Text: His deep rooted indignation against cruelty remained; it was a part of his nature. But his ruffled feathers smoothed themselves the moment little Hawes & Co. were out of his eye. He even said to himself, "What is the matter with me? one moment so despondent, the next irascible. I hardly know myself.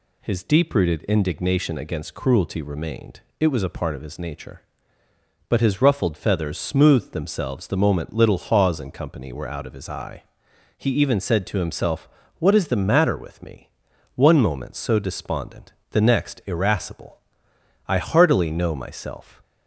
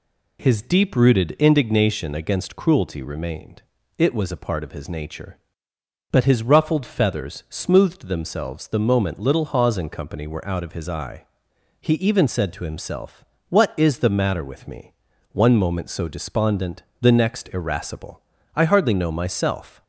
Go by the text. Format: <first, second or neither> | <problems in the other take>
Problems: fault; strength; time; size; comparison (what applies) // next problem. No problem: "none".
second | says "heartily" for "hardly"; at 17.9 s